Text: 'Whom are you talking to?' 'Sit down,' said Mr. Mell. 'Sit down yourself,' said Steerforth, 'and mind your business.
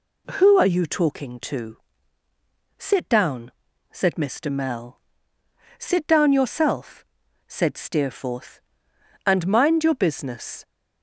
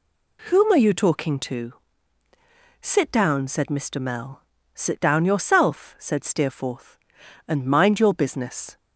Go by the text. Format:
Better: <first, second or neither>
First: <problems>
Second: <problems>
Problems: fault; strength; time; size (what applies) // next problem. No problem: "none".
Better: second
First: says "Who" for "Whom"; at 0.3 s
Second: none